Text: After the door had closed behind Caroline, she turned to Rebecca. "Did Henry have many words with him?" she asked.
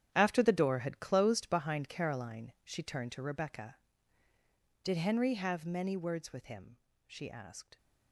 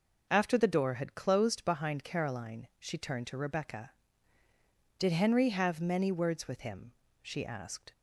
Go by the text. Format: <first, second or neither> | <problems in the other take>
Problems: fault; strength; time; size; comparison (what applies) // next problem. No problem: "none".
second | gets quieter; strong; throughout; 13 dB